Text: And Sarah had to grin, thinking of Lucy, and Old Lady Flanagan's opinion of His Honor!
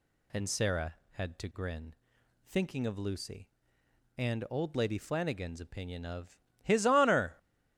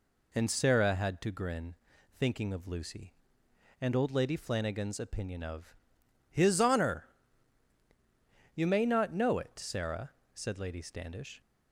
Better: first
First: pauses between "of" and "His"; slight; at 6.3 s; 0.24 s long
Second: pauses between "of" and "His"; noticeable; at 5.7 s; 0.53 s long // goes on to say "You may not know it Sarah said Lady Standish"; strong; from 8.5 s on; 2.8 s long

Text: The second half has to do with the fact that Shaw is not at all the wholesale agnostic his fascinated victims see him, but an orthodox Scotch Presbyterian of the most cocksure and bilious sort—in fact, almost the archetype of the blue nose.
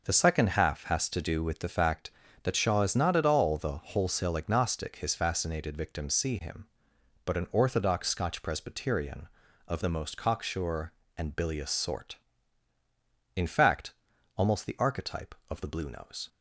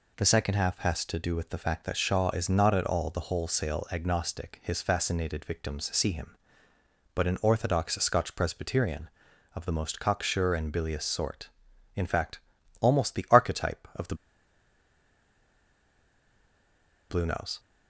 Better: first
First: none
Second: pauses between "the" and "blue"; strong; at 14.1 s; 2.9 s long

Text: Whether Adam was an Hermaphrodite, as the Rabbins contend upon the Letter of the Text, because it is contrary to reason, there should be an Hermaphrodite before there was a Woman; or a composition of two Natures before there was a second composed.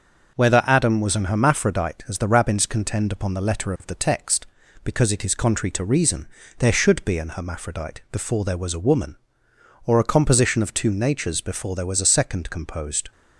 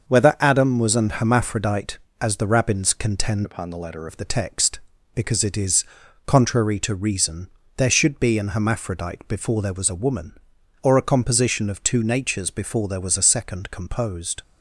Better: first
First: none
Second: starts louder than the rest; until 1.1 s; 6.5 dB // changes voice from "upon" to "Letter"; from 3.4 to 4.0 s; 0.6 s long // pauses between "is" and "contrary"; at 5.8 s; 0.42 s long

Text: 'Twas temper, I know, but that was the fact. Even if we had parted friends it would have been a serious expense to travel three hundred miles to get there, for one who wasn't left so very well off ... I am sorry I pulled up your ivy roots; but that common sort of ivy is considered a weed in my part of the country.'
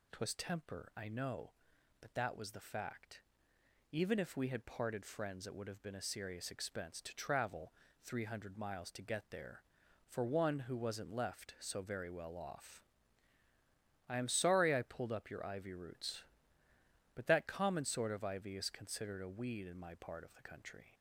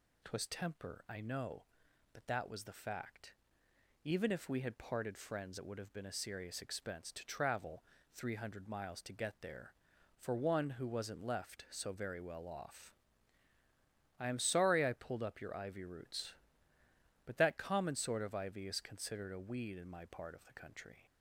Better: neither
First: pauses between "travel" and "three"; slight; at 7.7 s; 0.30 s long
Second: pauses between "travel" and "three"; slight; at 7.8 s; 0.30 s long

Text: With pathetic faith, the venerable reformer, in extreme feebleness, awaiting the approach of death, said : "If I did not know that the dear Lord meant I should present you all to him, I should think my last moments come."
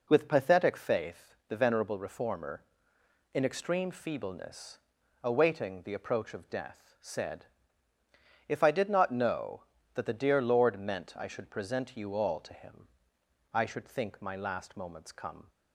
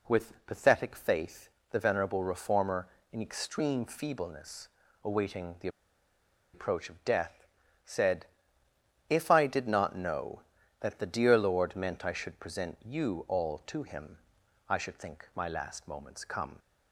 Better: first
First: none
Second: pauses between "the" and "approach"; noticeable; at 5.6 s; 0.85 s long

